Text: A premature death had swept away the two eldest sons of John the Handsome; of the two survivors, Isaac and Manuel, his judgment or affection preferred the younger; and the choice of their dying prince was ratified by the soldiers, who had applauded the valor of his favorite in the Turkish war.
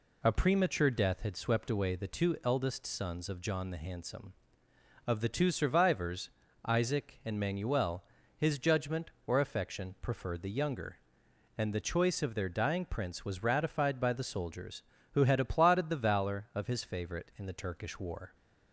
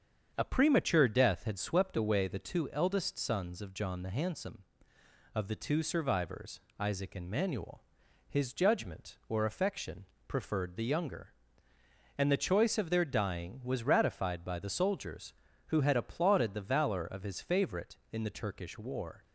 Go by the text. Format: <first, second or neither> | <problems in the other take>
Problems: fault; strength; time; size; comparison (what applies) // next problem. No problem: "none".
first | starts louder than the rest; strong; until 1.3 s; 7.5 dB // pauses between "affection" and "preferred"; slight; at 10.0 s; 0.20 s long // skips "prince"; at 13.6 s